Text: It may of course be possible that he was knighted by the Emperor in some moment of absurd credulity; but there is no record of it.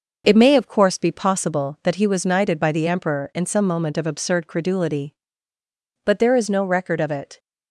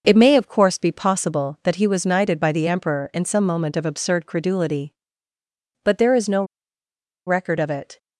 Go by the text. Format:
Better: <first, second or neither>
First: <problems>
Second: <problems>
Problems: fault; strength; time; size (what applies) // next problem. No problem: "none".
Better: first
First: none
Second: pauses between "no" and "record"; noticeable; at 6.4 s; 0.83 s long